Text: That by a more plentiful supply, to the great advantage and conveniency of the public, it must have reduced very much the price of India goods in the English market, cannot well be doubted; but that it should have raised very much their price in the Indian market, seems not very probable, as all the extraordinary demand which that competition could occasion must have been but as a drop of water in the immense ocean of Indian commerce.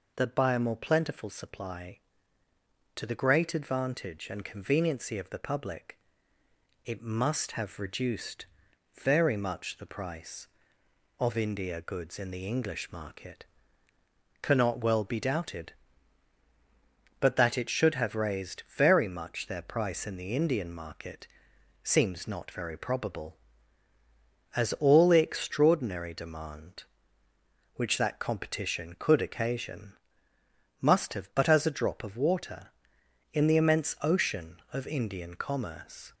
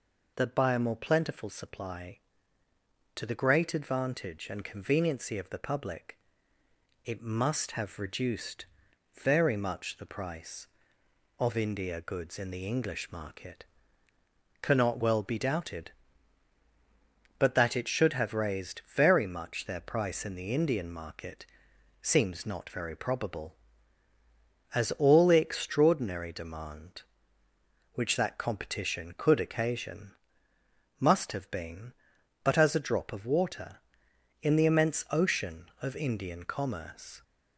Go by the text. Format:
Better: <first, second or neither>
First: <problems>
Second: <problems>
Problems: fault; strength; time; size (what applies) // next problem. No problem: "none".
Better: second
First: pauses between "reduced" and "very"; noticeable; at 8.4 s; 0.56 s long // pauses between "occasion" and "must"; noticeable; at 29.9 s; 0.90 s long // skips "been"; at 31.3 s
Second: pauses between "reduced" and "very"; noticeable; at 8.6 s; 0.56 s long // pauses between "occasion" and "must"; noticeable; at 30.1 s; 0.90 s long